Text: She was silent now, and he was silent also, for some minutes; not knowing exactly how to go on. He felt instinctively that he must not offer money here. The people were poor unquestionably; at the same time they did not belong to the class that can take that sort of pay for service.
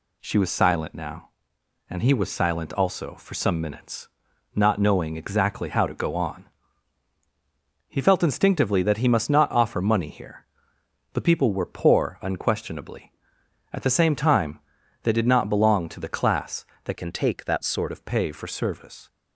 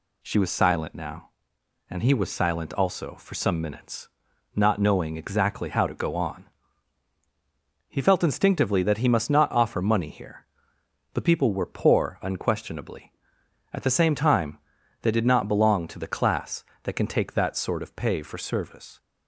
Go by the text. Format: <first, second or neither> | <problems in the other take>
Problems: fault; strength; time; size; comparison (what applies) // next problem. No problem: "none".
second | pauses between "time" and "they"; noticeable; at 14.5 s; 0.46 s long; noticeable in the second // changes voice from "can" to "sort"; from 16.9 to 17.9 s; 1.0 s long